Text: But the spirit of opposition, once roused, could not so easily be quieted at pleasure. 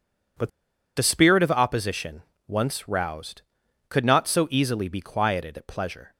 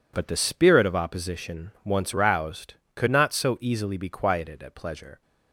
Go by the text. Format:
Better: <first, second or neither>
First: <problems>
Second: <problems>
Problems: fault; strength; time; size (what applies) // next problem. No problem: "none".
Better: second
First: pauses between "But" and "the"; noticeable; at 0.5 s; 0.47 s long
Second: none